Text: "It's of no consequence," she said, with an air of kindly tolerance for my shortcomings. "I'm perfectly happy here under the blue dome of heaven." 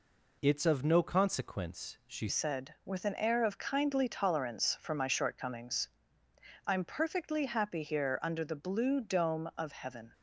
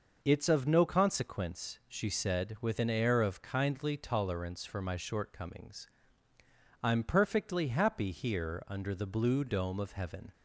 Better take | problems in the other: second | changes voice at "said"; from 2.2 s on; 7.9 s long

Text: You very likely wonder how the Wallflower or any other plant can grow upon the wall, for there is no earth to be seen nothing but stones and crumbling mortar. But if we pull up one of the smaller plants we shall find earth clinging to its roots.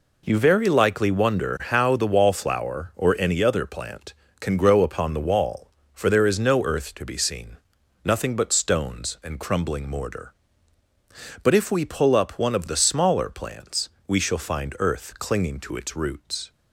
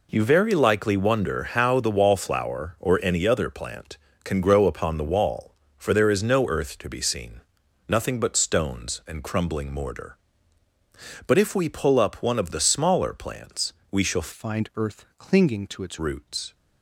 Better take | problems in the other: first | pauses between "seen" and "nothing"; noticeable; at 7.4 s; 0.46 s long; noticeable in the first // pauses between "plants" and "we"; slight; at 13.7 s; 0.18 s long; slight in the first // changes voice from "find" to "its"; from 14.3 to 15.9 s; 1.6 s long

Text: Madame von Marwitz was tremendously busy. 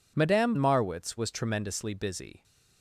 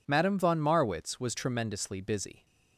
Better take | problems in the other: second | skips "von"; at 0.5 s

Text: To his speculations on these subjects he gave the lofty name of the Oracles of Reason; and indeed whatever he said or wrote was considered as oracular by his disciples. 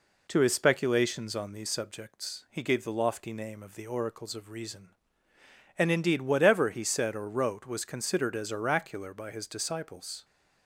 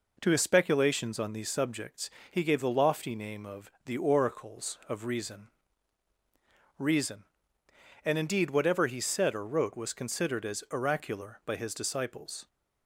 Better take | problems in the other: first | pauses between "subjects" and "he"; slight; at 2.1 s; 0.21 s long // says "Reason" twice; at 6.7 s

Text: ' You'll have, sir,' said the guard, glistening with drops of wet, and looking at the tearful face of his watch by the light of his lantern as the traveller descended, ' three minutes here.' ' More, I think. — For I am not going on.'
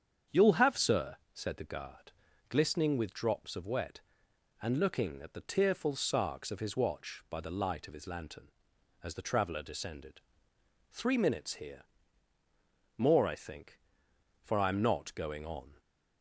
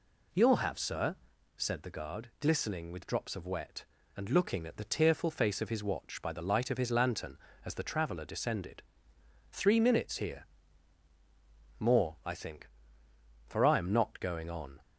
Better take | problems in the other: second | starts louder than the rest; strong; until 1.4 s; 8 dB // says "sarks" for "face"; at 5.9 s

